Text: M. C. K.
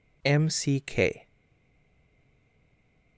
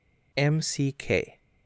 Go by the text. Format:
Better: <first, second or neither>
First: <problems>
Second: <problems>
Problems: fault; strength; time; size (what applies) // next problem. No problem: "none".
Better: second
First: stays silent after the last word; noticeable; from 1.2 s on; 1.9 s long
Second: none